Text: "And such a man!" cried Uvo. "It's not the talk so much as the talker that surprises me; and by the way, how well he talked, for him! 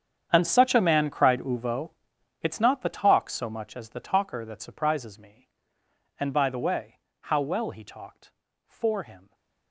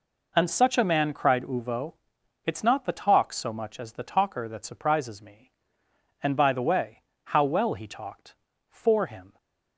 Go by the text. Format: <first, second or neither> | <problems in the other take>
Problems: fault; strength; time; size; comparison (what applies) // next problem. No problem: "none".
second | gets quieter; strong; throughout; 17 dB